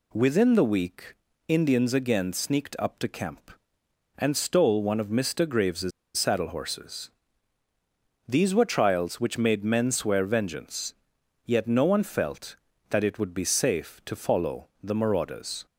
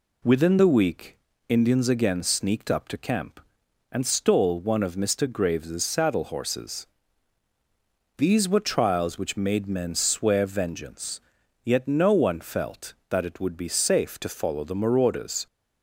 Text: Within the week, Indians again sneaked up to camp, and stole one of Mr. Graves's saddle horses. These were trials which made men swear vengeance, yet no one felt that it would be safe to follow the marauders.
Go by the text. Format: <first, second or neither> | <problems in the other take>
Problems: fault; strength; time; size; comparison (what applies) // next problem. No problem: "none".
second | pauses between "Graves's" and "saddle"; slight; at 5.9 s; 0.26 s long